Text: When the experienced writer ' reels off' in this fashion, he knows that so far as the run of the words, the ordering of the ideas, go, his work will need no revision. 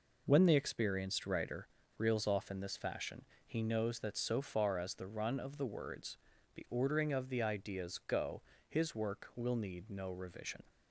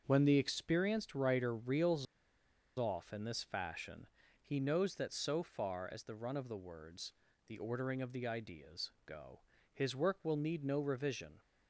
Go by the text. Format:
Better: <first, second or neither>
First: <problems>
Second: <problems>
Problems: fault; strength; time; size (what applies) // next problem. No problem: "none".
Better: first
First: none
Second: starts louder than the rest; until 1.0 s; 7 dB // pauses between "reels" and "off"; noticeable; at 2.0 s; 0.72 s long